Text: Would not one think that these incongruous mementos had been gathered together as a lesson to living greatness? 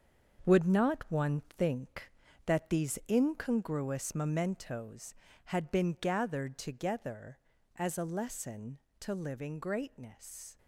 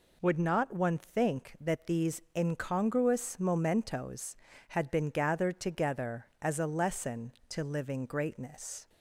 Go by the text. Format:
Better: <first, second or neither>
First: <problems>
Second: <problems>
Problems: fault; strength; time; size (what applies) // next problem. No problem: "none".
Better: second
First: gets quieter; strong; throughout; 9.5 dB // pauses between "one" and "think"; slight; at 1.4 s; 0.16 s long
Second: none